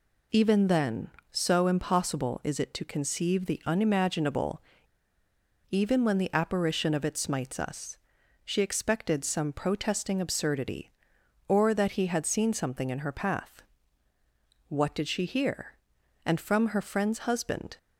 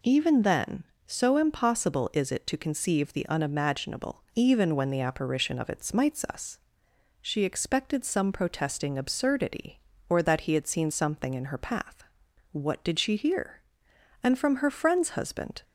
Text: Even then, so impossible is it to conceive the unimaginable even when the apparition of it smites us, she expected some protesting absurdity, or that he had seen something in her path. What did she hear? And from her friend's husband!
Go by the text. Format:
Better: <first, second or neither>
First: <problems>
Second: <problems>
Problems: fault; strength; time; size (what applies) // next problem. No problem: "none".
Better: second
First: pauses between "unimaginable" and "even"; at 4.6 s; 1.0 s long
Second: none